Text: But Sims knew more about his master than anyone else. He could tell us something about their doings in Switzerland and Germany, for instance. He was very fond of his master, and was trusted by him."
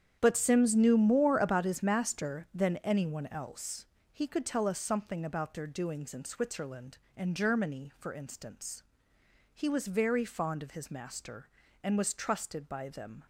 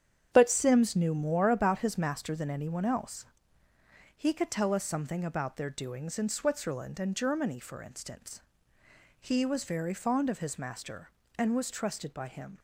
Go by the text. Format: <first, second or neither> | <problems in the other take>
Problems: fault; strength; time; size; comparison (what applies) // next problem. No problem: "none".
second | starts louder than the rest; strong; until 1.2 s; 9 dB; strong in the second // says "them" for "him"; at 12.8 s